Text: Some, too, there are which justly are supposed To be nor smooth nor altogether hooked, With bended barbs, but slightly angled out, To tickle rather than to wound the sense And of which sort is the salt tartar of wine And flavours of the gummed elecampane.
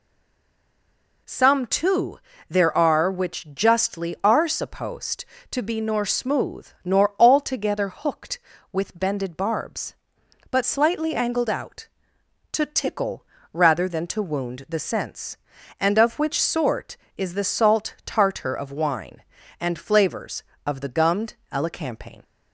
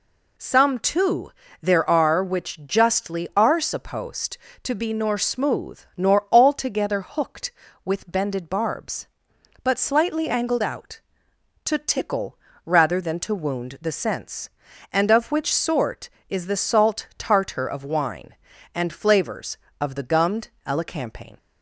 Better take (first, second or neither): second